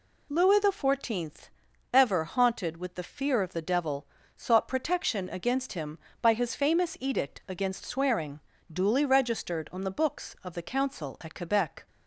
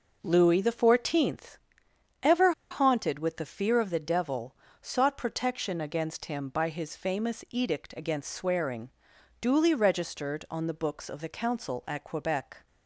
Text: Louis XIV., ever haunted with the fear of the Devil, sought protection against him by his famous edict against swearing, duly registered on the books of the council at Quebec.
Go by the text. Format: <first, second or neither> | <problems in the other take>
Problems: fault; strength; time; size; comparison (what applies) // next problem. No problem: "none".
first | pauses between "ever" and "haunted"; slight; at 2.5 s; 0.19 s long